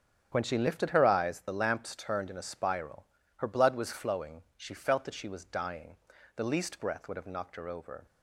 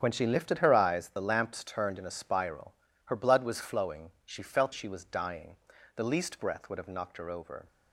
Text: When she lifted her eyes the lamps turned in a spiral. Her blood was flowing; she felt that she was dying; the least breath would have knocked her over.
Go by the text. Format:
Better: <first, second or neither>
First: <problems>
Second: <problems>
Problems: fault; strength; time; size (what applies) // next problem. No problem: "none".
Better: first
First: starts louder than the rest; until 1.3 s; 7 dB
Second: starts louder than the rest; strong; until 1.0 s; 7 dB // skips "that"; at 4.7 s